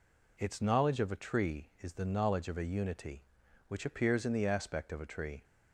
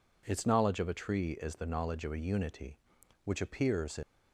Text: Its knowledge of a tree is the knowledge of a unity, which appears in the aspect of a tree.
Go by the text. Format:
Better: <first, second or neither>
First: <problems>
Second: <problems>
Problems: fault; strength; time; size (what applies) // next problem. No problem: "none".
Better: first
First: none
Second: stops before "the aspect of a tree"; at 4.0 s